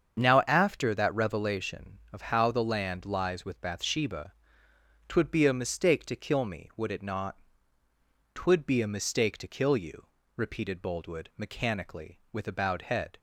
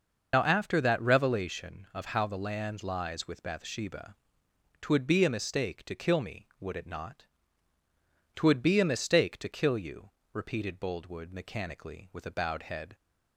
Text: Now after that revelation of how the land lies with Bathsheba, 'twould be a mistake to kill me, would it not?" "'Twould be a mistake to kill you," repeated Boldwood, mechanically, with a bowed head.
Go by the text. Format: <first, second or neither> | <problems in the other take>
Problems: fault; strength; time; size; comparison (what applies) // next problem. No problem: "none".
first | loses the start of "Now"; at 0.3 s; 65 ms // starts louder than the rest; noticeable; until 1.3 s; 6 dB; strong in the first